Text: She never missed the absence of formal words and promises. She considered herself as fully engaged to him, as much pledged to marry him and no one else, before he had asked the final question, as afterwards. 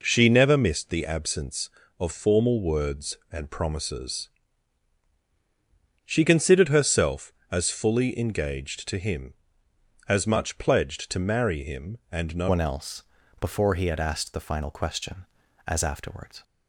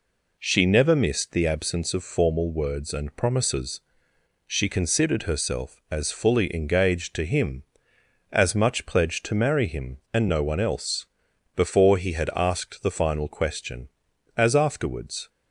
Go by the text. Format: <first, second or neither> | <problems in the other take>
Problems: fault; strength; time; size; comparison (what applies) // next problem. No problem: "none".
second | changes voice at "one"; from 12.4 s on; 4.0 s long